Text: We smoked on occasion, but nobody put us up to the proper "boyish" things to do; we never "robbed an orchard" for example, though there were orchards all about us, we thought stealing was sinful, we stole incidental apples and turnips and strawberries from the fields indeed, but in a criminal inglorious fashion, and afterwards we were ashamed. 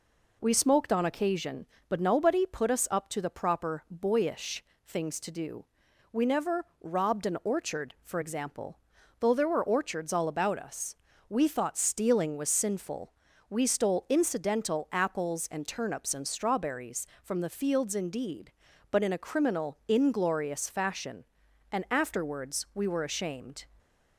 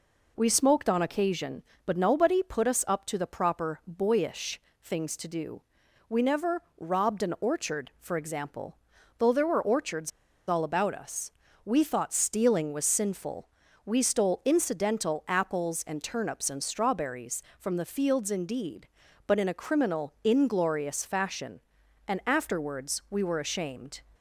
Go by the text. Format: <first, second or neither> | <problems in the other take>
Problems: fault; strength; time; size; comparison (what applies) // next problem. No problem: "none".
first | pauses between "boyish" and "things"; slight; at 4.5 s; 0.24 s long; slight in the first // pauses between "never" and "robbed"; slight; at 6.6 s; 0.16 s long; slight in the first // pauses between "orchards" and "all"; at 10.1 s; 0.37 s long